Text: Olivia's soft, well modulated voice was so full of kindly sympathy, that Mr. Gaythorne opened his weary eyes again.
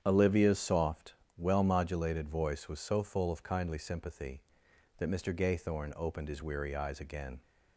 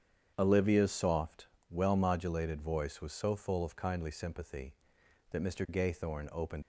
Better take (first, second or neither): first